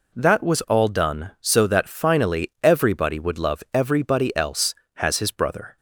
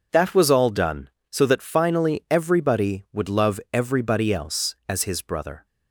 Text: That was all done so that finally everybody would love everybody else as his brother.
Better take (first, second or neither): second